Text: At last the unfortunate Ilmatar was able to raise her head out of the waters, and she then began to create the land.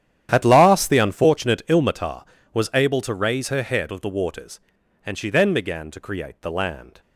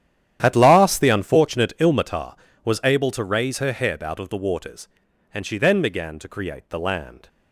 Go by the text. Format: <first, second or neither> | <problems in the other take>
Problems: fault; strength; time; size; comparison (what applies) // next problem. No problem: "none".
second | starts louder than the rest; strong; until 1.3 s; 10.5 dB; strong in the second // skips "out"; at 3.9 s